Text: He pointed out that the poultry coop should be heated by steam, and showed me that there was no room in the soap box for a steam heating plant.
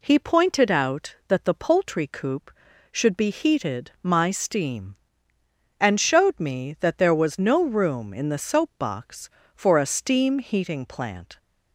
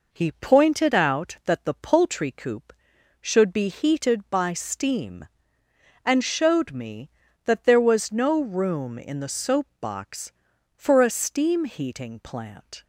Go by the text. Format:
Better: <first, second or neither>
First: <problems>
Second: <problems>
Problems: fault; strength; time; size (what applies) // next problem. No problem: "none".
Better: second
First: says "my" for "by"; at 4.0 s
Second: none